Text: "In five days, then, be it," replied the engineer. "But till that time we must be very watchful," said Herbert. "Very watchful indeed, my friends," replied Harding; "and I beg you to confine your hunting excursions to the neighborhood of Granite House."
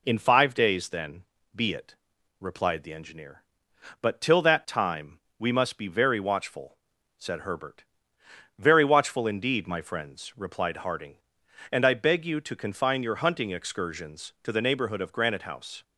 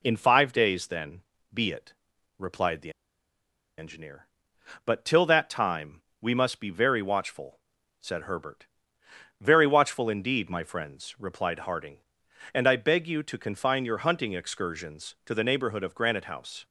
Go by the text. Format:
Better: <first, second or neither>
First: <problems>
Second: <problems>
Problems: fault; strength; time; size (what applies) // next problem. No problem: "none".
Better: first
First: pauses between "time" and "we"; slight; at 5.1 s; 0.20 s long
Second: pauses between "the" and "engineer"; noticeable; at 2.8 s; 0.88 s long // pauses between "time" and "we"; slight; at 6.0 s; 0.20 s long